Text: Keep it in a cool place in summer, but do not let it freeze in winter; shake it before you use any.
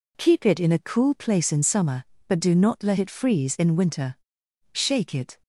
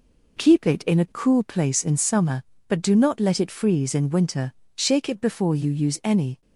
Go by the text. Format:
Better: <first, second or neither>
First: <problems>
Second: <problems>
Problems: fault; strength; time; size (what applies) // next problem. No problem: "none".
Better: second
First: stops before "before you use any"; at 5.4 s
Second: none